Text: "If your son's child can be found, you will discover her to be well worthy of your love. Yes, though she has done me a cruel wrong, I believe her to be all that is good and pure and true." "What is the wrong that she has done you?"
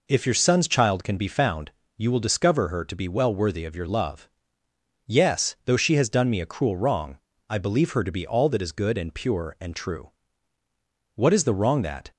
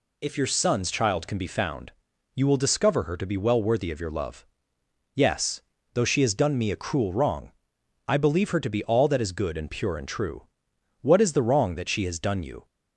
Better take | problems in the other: second | stops before "she has done you"; at 12.1 s

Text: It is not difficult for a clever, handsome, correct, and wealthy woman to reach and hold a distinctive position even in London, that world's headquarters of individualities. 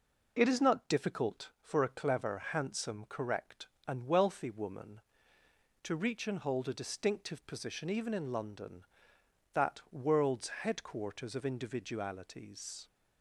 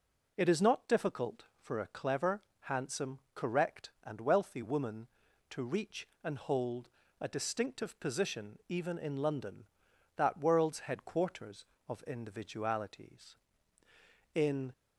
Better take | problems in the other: first | pauses between "hold" and "a"; slight; at 6.8 s; 0.32 s long // goes on to say "In"; slight; from 14.3 s on; 0.38 s long

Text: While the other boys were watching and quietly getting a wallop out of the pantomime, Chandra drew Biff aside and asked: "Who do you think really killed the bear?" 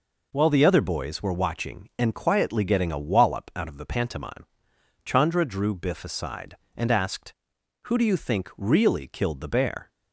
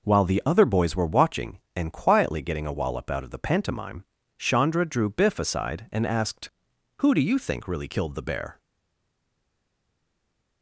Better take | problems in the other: first | stays silent after the last word; noticeable; from 8.5 s on; 2.1 s long

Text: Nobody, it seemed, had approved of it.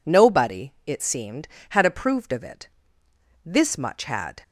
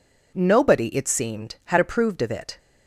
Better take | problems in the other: second | goes on to say "This much had"; noticeable; from 3.4 s on; 0.98 s long

